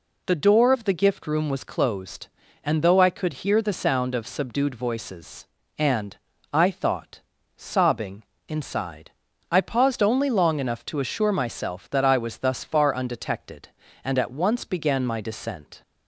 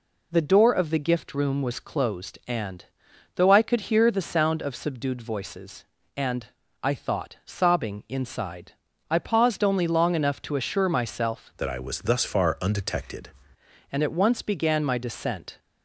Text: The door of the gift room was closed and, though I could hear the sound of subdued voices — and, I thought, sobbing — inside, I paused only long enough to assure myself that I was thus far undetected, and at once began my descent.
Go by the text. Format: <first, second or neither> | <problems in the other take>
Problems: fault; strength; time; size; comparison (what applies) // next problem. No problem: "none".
first | changes voice from "that" to "undetected"; from 11.5 to 13.2 s; 1.7 s long